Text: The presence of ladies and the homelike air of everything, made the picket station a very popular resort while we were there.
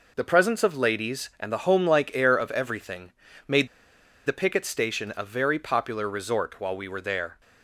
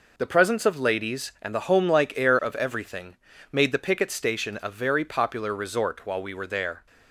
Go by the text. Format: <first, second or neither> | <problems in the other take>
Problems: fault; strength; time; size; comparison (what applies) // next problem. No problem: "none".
second | pauses between "made" and "the"; noticeable; at 3.6 s; 0.58 s long